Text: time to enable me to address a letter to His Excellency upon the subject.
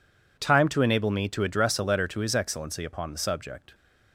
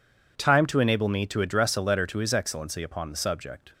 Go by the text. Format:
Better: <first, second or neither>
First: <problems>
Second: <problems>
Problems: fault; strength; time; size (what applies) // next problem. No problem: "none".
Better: neither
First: none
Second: none